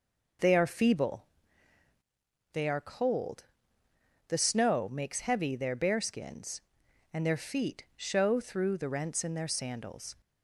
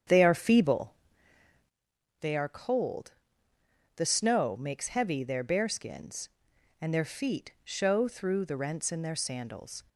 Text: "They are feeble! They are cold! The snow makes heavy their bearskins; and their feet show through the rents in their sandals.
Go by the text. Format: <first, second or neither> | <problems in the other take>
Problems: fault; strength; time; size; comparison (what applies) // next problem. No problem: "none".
first | starts louder than the rest; strong; until 1.8 s; 8 dB